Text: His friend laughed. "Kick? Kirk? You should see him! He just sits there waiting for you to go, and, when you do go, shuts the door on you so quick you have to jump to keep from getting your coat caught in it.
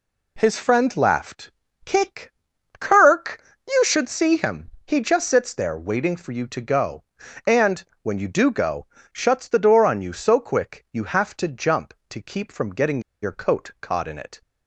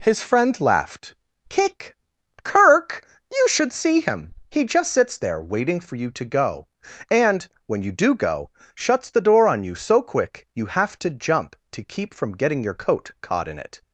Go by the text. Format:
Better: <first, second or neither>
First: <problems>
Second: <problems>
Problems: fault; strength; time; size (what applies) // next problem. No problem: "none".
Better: second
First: pauses between "getting" and "your"; slight; at 13.0 s; 0.21 s long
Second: none